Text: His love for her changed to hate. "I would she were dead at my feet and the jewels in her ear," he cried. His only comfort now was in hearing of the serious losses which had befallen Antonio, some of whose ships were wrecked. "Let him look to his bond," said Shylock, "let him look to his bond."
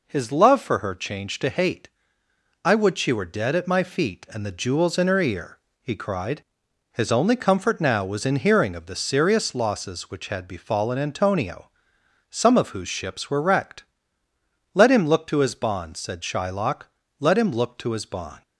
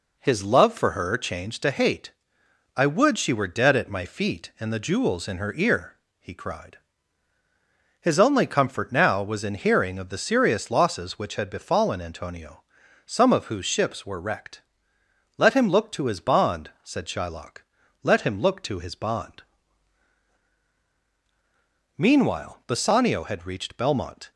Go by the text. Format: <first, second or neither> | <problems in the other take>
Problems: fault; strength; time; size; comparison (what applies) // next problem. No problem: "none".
first | goes on to say "Meanwhile Bassanio had reached Belmont"; strong; from 21.9 s on; 2.3 s long